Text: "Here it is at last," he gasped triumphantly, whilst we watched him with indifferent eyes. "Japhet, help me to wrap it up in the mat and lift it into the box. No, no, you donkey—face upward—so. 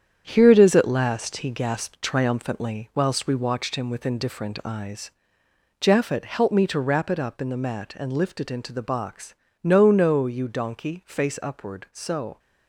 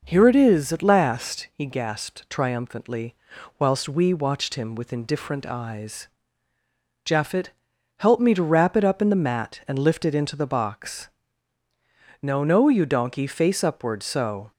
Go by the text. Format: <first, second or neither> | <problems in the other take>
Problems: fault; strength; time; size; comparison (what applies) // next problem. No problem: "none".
second | gets quieter; throughout; 7 dB